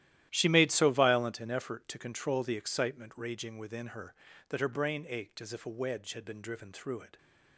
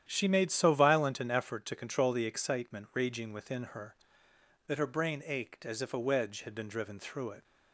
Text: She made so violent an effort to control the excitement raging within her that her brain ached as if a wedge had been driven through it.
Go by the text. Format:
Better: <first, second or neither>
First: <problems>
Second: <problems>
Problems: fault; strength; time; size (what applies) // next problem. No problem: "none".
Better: second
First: gets quieter; strong; throughout; 14.5 dB // starts louder than the rest; strong; until 1.3 s; 13 dB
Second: starts louder than the rest; strong; until 1.1 s; 10.5 dB